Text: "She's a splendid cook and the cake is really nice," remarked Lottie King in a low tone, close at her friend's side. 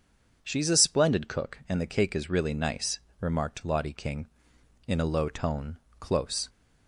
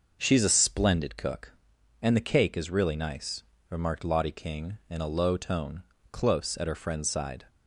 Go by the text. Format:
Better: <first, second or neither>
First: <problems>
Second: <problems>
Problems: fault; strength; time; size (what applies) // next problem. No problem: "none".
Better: second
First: stops before "at her friend's side"; at 6.4 s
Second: none